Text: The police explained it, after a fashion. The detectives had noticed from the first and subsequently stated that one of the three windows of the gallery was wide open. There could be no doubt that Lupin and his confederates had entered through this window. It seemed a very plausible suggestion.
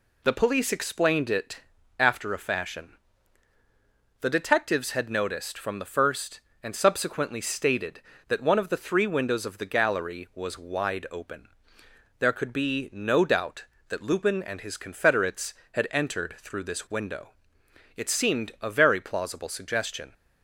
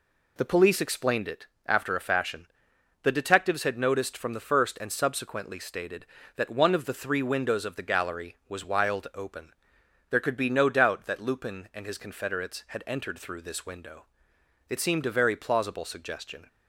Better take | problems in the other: first | says "wild" for "wide"; at 8.6 s

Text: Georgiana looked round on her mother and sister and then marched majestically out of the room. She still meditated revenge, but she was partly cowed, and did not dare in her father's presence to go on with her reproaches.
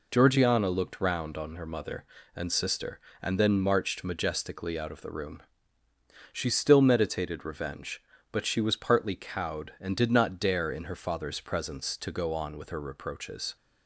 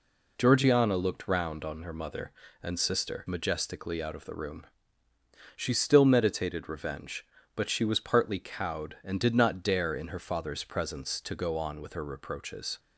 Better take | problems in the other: first | skips "and then marched"; at 3.2 s

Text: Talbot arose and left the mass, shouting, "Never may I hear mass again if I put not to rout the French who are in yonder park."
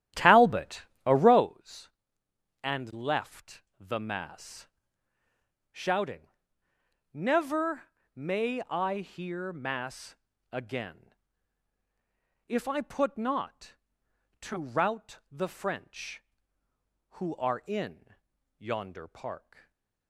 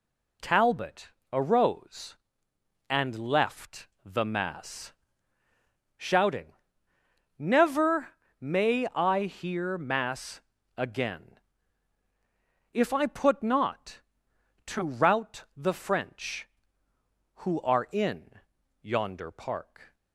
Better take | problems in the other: second | starts louder than the rest; strong; until 1.5 s; 12 dB // pauses between "Talbot" and "arose"; slight; at 0.8 s; 0.22 s long; slight in the second // pauses between "left" and "the"; slight; at 3.6 s; 0.18 s long; slight in the second // pauses between "Never" and "may"; slight; at 7.8 s; 0.26 s long; slight in the second // pauses between "mass" and "again"; slight; at 10.1 s; 0.36 s long; slight in the second // pauses between "again" and "if"; strong; at 11.1 s; 1.3 s long; strong in the second // pauses between "in" and "yonder"; at 18.1 s; 0.44 s long; also in the second // stays silent after the last word; slight; from 19.5 s on; 0.5 s long

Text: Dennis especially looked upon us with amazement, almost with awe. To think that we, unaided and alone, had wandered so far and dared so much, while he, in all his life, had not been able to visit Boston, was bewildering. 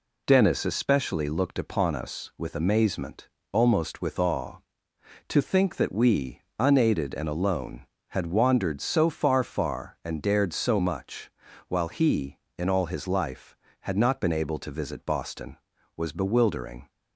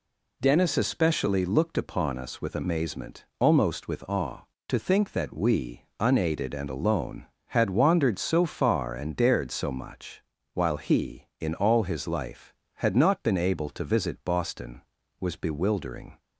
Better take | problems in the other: second | says "far" twice; at 9.4 s

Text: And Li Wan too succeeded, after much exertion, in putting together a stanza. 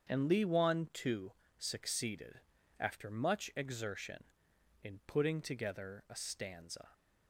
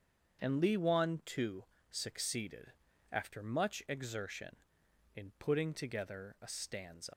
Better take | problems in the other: first | starts louder than the rest; strong; until 1.4 s; 7.5 dB; strong in the first // pauses between "too" and "succeeded"; slight; at 1.6 s; 0.24 s long; slight in the first // leaves "stanza" unfinished; at 7.1 s; 115 ms

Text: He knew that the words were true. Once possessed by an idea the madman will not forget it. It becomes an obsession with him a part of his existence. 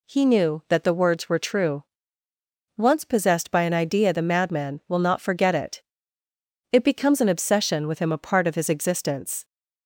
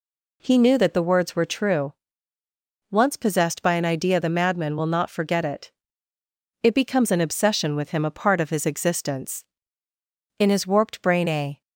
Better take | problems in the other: first | goes on to say "In his warped brain a"; noticeable; from 10.3 s on; 1.2 s long

